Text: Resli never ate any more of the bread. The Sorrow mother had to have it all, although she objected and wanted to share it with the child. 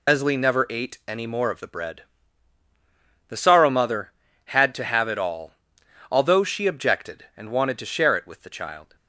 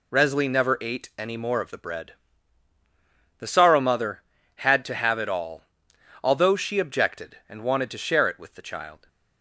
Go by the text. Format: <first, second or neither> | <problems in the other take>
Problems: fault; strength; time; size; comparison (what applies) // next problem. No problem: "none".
second | loses the start of "Resli"; at 0.0 s; 65 ms